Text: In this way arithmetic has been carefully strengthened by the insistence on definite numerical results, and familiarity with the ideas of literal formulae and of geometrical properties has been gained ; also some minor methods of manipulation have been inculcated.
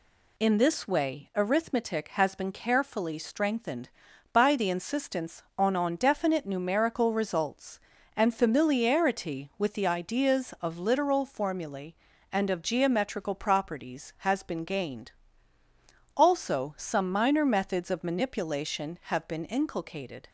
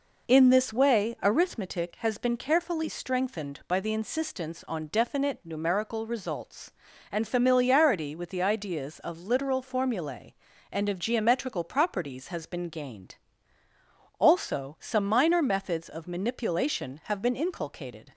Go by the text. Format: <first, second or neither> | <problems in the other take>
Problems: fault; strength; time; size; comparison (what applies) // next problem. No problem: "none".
second | says "on" twice; at 5.7 s